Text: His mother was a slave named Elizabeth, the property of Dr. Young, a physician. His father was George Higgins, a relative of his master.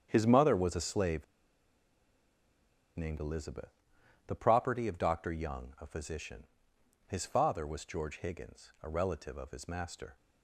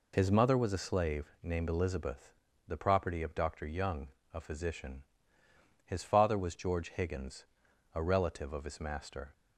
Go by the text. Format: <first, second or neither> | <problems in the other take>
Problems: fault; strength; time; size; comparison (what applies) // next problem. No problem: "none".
second | starts louder than the rest; strong; until 1.1 s; 8.5 dB // pauses between "slave" and "named"; strong; at 1.2 s; 1.7 s long